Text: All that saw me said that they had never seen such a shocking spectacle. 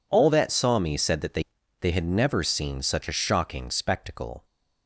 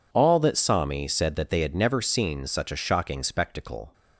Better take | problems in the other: second | says "they" twice; at 1.8 s

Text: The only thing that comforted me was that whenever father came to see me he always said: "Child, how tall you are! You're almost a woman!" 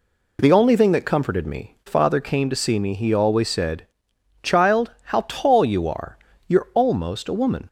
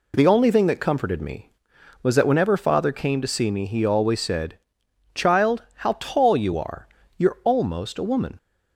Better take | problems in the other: second | skips "was that whenever"; at 1.8 s

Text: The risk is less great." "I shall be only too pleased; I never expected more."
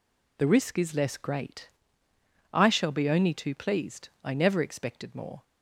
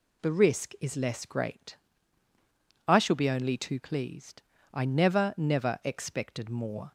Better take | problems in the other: first | says "never" twice; at 5.3 s

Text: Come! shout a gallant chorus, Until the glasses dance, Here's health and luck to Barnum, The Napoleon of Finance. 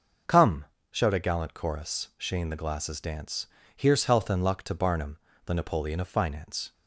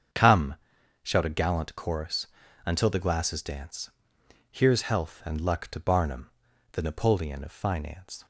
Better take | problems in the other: second | starts louder than the rest; noticeable; until 1.5 s; 6 dB; strong in the second // says "Shane" for "Until"; at 2.1 s

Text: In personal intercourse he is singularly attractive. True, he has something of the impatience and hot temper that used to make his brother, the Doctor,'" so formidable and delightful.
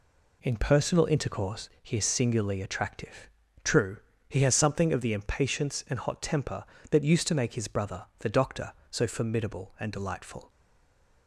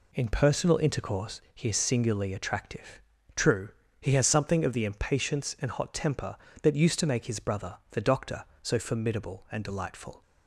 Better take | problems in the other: second | stays silent after the last word; slight; from 10.4 s on; 0.8 s long

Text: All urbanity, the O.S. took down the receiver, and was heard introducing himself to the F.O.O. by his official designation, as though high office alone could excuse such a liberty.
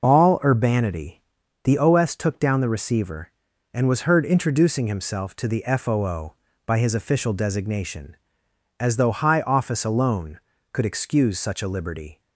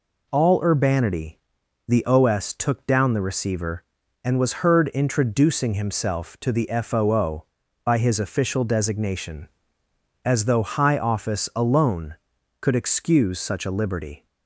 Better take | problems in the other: neither | none

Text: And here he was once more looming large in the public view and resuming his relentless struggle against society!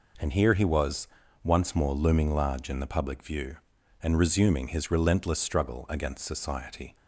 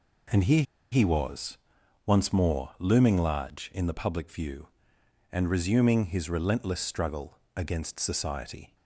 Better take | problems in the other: first | pauses between "here" and "he"; slight; at 0.6 s; 0.29 s long // pauses between "was" and "once"; noticeable; at 1.5 s; 0.50 s long; slight in the first // pauses between "struggle" and "against"; slight; at 7.3 s; 0.20 s long

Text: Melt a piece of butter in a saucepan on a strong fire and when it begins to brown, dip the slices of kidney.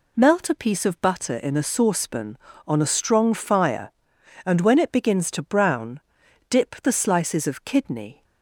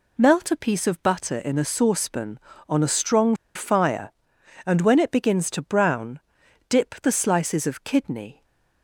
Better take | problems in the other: first | pauses between "strong" and "fire"; slight; at 3.3 s; 0.20 s long // stays silent after the last word; slight; from 8.3 s on; 0.5 s long

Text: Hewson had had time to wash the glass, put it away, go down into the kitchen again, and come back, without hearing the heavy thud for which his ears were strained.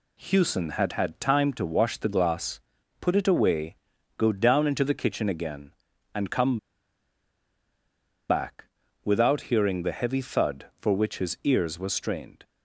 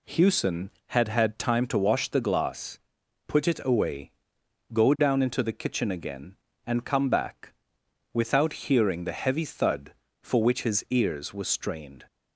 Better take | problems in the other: second | pauses between "come" and "back"; strong; at 6.5 s; 1.7 s long

